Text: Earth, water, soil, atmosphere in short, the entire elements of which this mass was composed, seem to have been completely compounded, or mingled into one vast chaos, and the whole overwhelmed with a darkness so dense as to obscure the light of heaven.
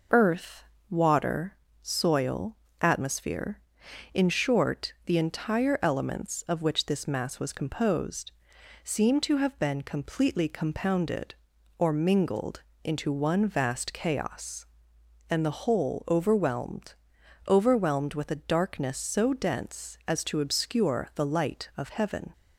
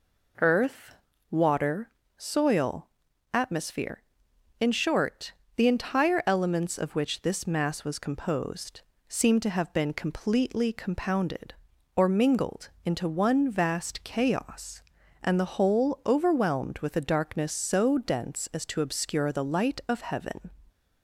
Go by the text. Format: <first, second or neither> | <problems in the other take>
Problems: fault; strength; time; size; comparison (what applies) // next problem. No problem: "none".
second | pauses between "mingled" and "into"; slight; at 12.6 s; 0.18 s long; slight in the second // says "overwhelmed" twice; at 17.4 s